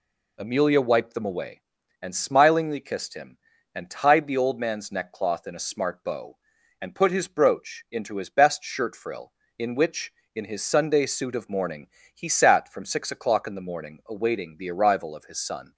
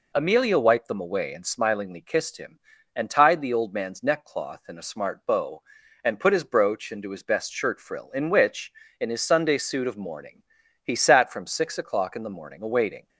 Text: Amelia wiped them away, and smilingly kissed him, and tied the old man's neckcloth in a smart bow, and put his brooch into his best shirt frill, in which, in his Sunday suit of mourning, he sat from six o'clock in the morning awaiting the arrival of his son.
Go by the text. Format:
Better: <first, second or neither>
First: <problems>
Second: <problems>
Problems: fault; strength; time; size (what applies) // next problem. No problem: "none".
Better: first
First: none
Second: stops before "the arrival of his son"; at 13.0 s